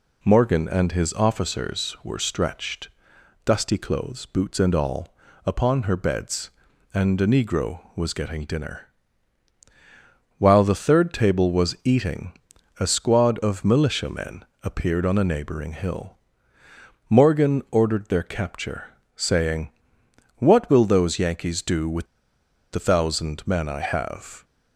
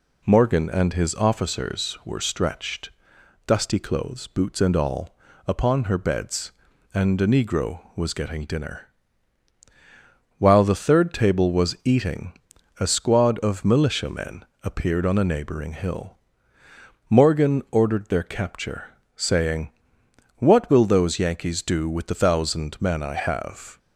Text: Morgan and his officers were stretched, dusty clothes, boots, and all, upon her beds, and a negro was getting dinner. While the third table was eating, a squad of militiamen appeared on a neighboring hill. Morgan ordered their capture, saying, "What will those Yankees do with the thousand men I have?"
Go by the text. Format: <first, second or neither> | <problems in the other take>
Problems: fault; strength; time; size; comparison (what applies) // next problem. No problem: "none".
second | pauses between "militiamen" and "appeared"; slight; at 14.4 s; 0.18 s long; slight in the second // pauses between "with" and "the"; noticeable; at 22.0 s; 0.66 s long